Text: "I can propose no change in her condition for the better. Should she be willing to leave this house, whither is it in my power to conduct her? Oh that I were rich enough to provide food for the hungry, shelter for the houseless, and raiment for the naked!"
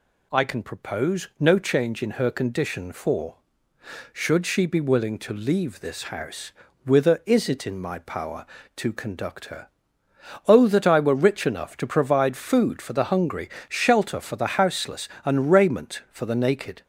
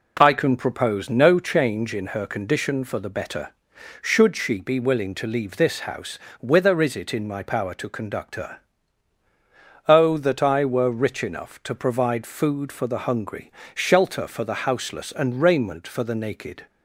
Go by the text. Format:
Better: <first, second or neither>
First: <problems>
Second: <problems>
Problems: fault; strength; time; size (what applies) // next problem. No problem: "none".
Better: second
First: skips "the better"; at 3.7 s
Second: none